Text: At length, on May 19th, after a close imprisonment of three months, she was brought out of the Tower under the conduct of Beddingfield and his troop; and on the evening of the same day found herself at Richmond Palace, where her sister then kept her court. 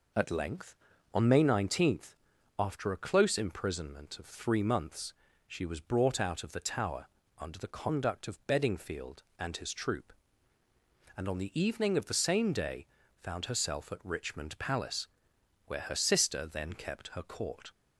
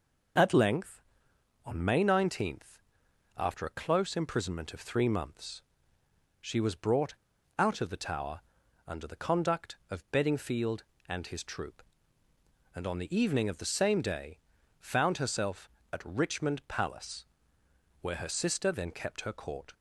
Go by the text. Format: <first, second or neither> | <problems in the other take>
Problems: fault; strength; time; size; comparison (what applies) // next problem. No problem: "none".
first | pauses between "brought" and "out"; at 7.1 s; 0.44 s long // pauses between "Tower" and "under"; noticeable; at 8.3 s; 0.48 s long; slight in the first // pauses between "day" and "found"; at 14.3 s; 0.42 s long; slight in the first